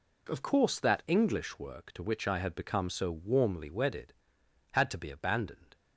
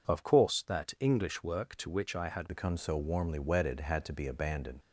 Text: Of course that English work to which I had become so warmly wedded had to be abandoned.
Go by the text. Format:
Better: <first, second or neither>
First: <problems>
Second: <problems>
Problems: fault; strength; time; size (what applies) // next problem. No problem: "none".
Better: first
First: none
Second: changes voice at "become"; from 2.4 s on; 2.3 s long